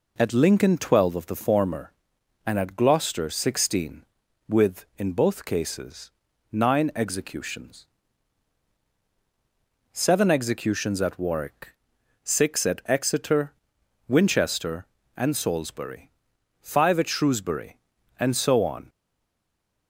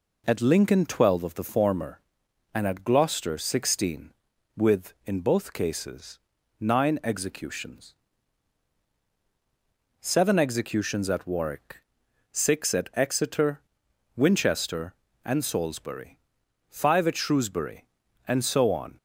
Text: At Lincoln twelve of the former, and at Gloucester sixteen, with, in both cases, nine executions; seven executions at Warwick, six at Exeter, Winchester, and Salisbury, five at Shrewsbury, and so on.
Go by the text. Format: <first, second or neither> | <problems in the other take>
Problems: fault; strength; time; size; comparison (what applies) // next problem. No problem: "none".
second | stays silent after the last word; from 18.8 s on; 1.0 s long